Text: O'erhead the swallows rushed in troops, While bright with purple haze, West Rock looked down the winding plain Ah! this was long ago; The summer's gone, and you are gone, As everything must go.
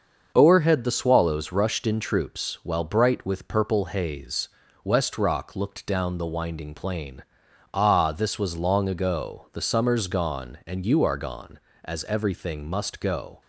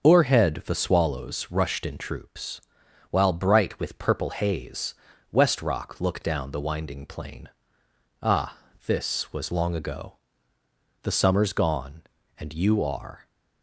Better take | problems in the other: first | starts louder than the rest; until 1.0 s; 7 dB; also in the first // pauses between "plain" and "Ah"; noticeable; at 7.4 s; 0.74 s long; noticeable in the first // stops before "gone As everything must go"; at 13.2 s

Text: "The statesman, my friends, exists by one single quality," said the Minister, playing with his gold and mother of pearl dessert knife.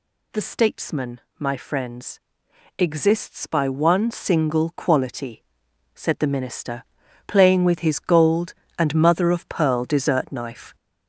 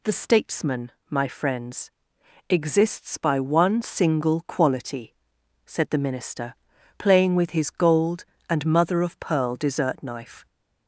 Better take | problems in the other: second | gets louder; noticeable; throughout; 5.5 dB

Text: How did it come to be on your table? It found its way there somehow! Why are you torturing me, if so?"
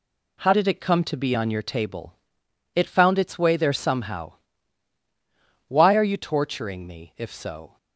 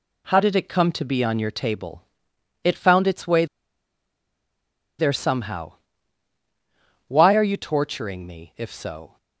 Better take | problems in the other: first | pauses between "way" and "there"; strong; at 3.4 s; 1.5 s long

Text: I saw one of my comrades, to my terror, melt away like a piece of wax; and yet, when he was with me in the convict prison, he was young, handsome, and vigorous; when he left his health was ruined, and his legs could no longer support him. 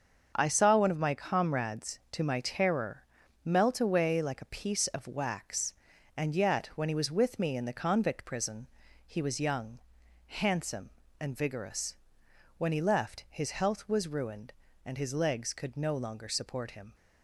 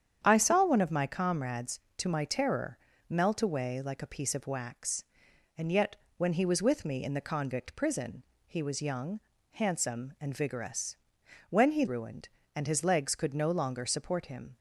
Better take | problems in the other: first | starts louder than the rest; strong; until 1.2 s; 8.5 dB; also in the first // skips "left his health was"; at 11.8 s

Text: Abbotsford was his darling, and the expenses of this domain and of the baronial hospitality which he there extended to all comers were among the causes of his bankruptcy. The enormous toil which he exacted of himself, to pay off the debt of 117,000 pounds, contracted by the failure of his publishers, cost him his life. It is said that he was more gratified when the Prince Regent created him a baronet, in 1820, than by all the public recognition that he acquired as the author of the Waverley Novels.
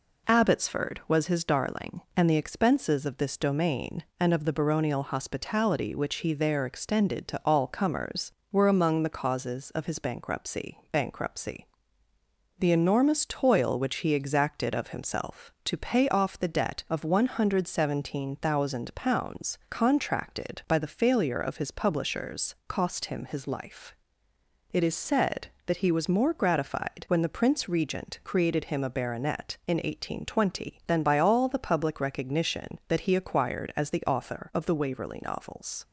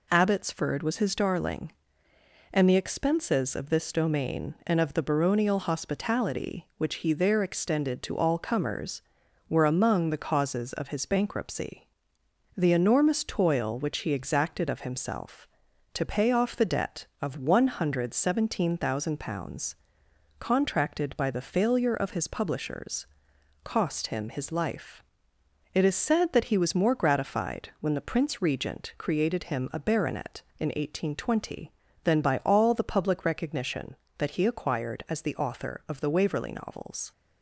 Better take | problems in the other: second | says "bankruptcy" twice; at 10.9 s

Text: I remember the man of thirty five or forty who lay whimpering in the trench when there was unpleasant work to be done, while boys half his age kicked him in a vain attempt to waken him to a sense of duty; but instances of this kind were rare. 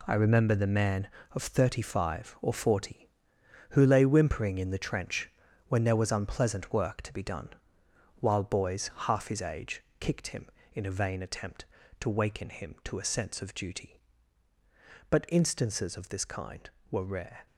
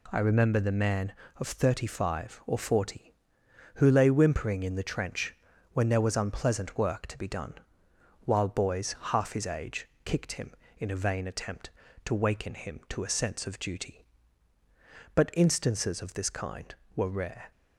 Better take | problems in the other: second | gets quieter; strong; throughout; 9 dB // pauses between "trench" and "when"; at 5.2 s; 0.38 s long; also in the second // pauses between "age" and "kicked"; slight; at 9.8 s; 0.16 s long; slight in the second

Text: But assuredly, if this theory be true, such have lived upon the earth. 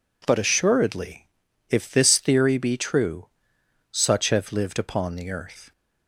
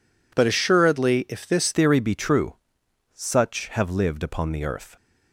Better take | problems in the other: first | changes voice at "theory"; from 1.7 s on; 3.2 s long

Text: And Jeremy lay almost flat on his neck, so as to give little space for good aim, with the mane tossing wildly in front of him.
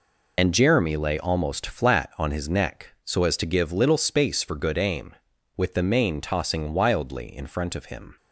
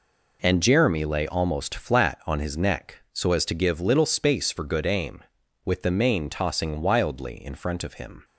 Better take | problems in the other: second | loses the start of "And"; at 0.3 s; 50 ms

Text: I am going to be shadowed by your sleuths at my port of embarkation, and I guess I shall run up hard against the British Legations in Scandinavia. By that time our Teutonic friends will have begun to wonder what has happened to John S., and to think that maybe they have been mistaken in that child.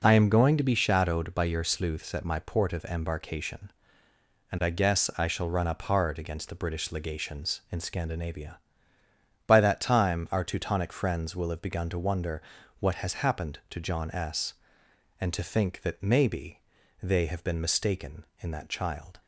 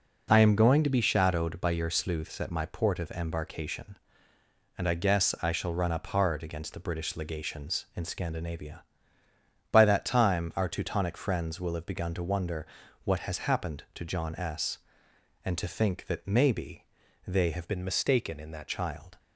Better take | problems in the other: first | pauses between "wonder" and "what"; at 12.6 s; 0.38 s long; also in the first // pauses between "maybe" and "they"; at 16.8 s; 0.42 s long; also in the first // changes voice from "been" to "that"; from 17.6 to 18.6 s; 1.0 s long

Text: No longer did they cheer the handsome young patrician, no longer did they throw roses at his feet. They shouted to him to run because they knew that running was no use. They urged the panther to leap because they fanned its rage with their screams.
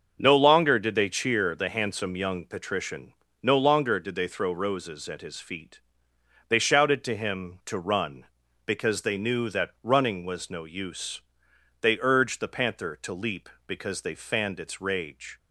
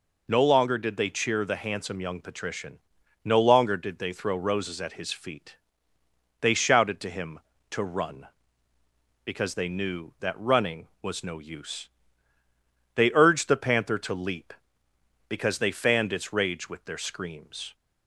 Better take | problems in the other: second | starts louder than the rest; until 1.2 s; 6.5 dB // stops before "with their screams"; at 15.3 s

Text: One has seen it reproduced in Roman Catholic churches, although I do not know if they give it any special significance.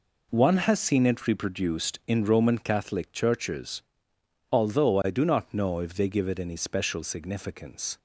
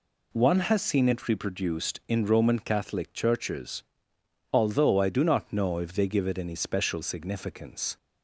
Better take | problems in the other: second | gets quieter; strong; throughout; 9 dB

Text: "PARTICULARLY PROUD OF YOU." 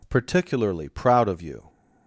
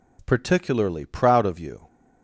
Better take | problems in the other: neither | none

